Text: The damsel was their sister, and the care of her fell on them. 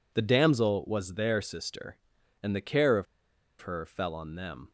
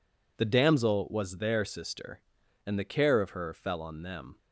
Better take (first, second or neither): second